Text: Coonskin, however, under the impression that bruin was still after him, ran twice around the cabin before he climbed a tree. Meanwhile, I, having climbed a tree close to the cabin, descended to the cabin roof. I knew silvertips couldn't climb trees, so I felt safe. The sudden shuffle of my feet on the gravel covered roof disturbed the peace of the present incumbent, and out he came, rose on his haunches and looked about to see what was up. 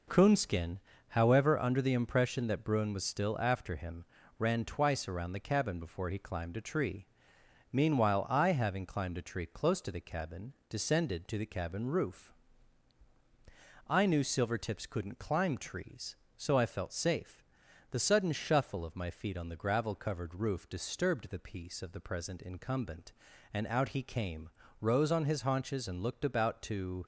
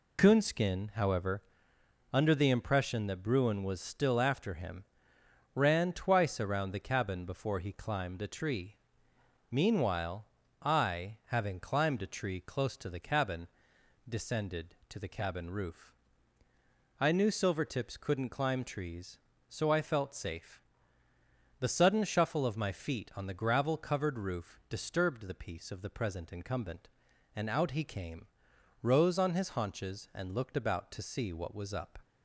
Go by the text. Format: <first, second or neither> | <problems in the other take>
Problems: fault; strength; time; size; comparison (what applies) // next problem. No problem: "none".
second | stops before "see what was up"; at 27.0 s